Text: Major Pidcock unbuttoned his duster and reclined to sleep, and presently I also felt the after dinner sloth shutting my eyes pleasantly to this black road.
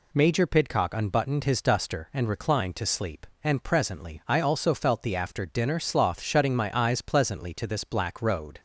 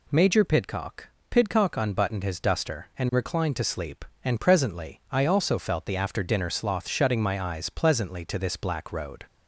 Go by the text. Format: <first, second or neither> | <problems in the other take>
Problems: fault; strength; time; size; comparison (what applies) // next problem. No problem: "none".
first | says "Pidcock" twice; at 1.2 s